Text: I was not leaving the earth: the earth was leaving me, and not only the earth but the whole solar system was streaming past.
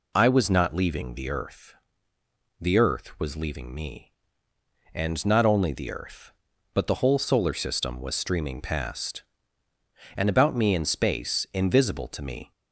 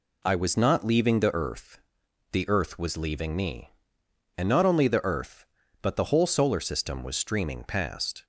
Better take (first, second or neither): second